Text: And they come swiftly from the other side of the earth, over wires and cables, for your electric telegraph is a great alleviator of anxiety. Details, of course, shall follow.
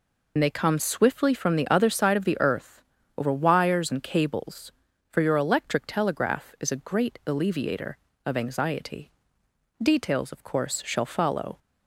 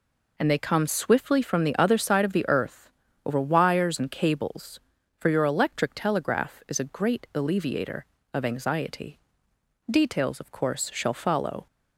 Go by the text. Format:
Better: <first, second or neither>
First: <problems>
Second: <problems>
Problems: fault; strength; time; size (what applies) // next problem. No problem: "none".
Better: second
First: loses the start of "And"; at 0.3 s; 55 ms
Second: none